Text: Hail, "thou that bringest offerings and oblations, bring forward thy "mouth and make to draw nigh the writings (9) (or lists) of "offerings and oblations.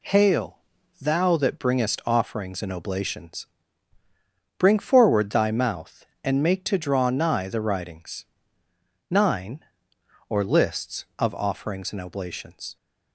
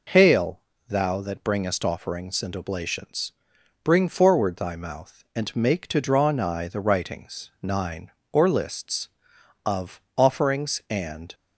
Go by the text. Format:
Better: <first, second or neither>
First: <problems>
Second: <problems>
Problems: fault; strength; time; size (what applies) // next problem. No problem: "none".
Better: first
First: none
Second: pauses between "of" and "offerings"; slight; at 9.9 s; 0.16 s long // stops before "oblations"; at 11.3 s